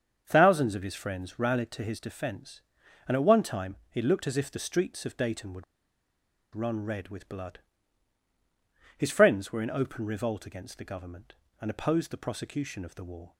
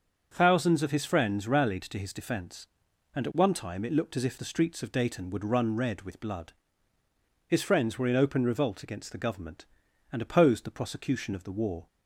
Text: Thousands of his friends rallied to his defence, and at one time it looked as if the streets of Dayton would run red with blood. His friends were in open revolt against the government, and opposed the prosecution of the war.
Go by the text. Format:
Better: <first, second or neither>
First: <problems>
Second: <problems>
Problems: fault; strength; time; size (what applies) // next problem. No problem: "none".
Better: second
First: starts louder than the rest; until 1.2 s; 7 dB // pauses between "time" and "it"; slight; at 3.7 s; 0.16 s long // pauses between "would" and "run"; noticeable; at 5.6 s; 0.91 s long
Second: starts louder than the rest; until 1.3 s; 7 dB